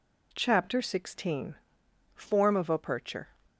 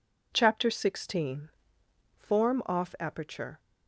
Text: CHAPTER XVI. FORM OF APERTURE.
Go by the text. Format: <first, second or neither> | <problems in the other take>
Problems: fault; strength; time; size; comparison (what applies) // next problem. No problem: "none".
first | says "Off" for "OF"; at 2.6 s